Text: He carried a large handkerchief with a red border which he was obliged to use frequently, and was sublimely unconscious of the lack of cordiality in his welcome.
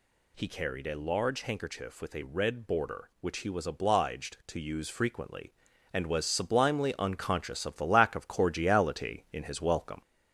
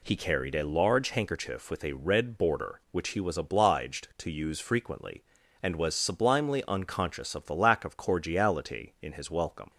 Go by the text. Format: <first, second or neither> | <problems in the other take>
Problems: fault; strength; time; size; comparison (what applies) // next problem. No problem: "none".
second | gets louder; slight; throughout; 3.5 dB